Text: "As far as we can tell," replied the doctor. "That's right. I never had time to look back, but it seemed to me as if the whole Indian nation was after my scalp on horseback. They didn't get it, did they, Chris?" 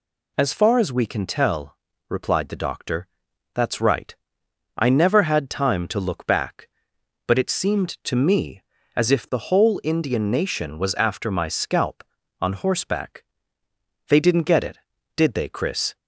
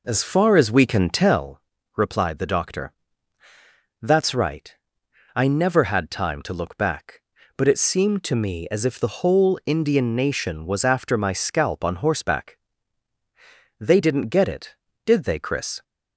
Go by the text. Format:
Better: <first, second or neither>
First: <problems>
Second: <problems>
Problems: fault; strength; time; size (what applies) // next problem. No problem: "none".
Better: first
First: none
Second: starts louder than the rest; noticeable; until 1.4 s; 4 dB